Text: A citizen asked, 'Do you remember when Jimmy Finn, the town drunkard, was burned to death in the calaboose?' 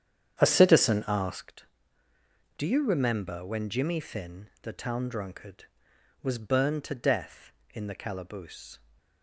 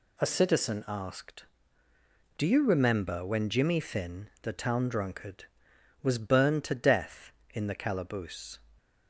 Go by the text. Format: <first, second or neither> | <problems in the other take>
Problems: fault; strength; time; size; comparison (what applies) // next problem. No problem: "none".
second | starts louder than the rest; strong; until 1.5 s; 9 dB